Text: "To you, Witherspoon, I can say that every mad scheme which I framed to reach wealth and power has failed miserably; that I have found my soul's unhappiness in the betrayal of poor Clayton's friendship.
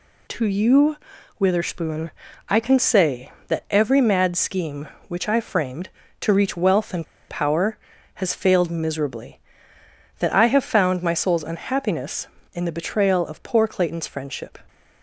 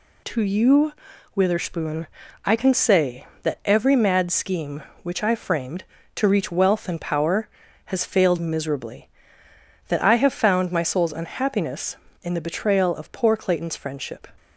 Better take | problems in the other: second | pauses between "and" and "power"; slight; at 7.0 s; 0.24 s long

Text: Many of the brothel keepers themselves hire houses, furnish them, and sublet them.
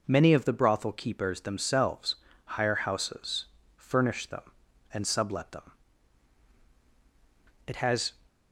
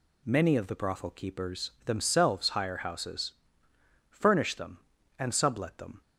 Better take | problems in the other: second | pauses between "themselves" and "hire"; slight; at 2.1 s; 0.28 s long // goes on to say "It has"; slight; from 7.6 s on; 0.48 s long

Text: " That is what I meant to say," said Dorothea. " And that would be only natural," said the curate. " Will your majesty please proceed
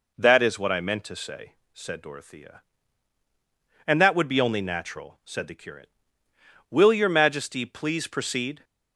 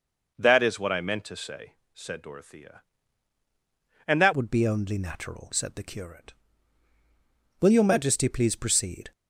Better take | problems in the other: first | changes voice at "would"; from 4.3 s on; 4.8 s long

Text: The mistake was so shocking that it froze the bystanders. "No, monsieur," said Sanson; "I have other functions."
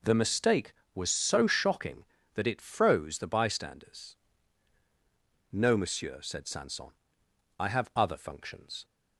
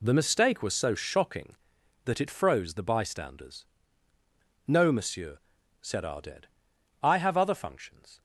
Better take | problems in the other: first | says "Arded" for "Sanson"; at 6.0 s

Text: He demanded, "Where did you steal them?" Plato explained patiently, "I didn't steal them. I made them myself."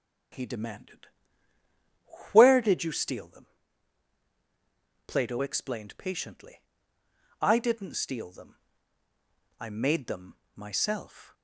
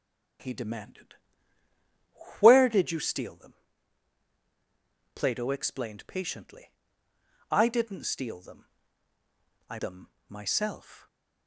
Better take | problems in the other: first | starts louder than the rest; strong; until 2.6 s; 9 dB; strong in the first // skips "made"; at 9.7 s // pauses between "them" and "myself"; slight; at 10.1 s; 0.18 s long; slight in the first // stays silent after the last word; slight; from 10.9 s on; 0.5 s long

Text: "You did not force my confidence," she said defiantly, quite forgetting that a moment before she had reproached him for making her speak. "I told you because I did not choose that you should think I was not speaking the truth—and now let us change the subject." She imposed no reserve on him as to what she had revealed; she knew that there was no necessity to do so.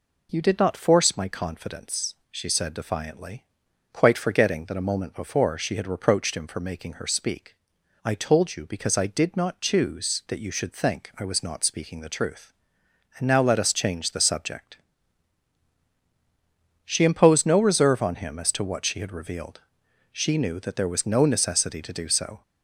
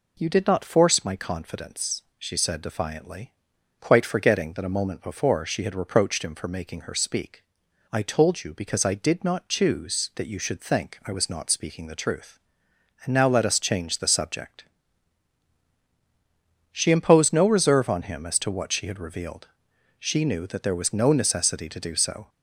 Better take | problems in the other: neither | none

